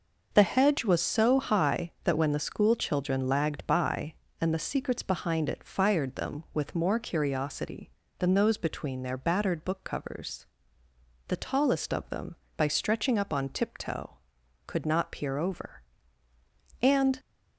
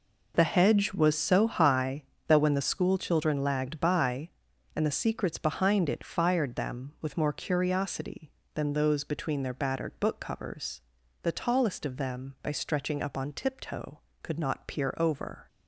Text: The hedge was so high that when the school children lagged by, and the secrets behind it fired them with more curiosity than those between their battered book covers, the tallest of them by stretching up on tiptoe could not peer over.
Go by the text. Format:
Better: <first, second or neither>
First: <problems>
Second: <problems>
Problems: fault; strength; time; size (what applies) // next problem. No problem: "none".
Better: second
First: starts louder than the rest; noticeable; until 1.3 s; 6 dB // goes on to say "And"; slight; from 16.8 s on; 0.38 s long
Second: none